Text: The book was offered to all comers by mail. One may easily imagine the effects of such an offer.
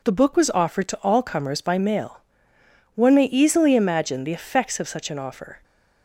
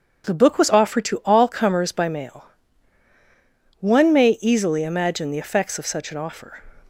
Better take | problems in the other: neither | none

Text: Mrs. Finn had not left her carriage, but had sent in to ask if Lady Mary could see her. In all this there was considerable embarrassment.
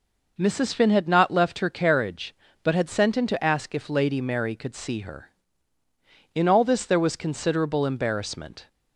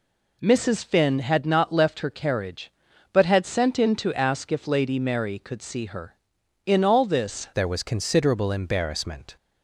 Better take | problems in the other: first | changes voice at "there"; from 7.5 s on; 1.8 s long

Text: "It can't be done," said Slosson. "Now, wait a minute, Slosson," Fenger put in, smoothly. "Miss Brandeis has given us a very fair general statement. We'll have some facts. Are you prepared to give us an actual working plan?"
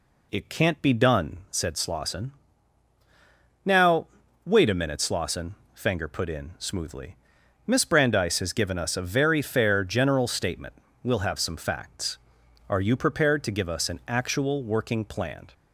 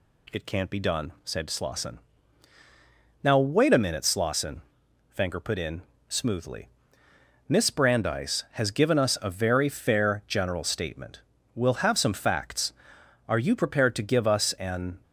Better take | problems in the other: first | stops before "actual working plan"; at 15.0 s

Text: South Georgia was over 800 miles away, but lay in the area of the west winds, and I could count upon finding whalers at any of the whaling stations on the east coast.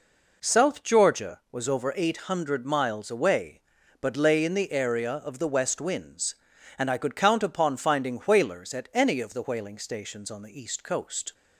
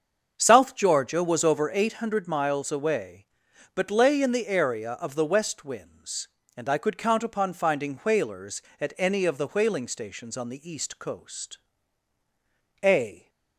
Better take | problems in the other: first | starts louder than the rest; until 1.3 s; 7 dB // goes on to say "A"; slight; from 12.8 s on; 0.46 s long

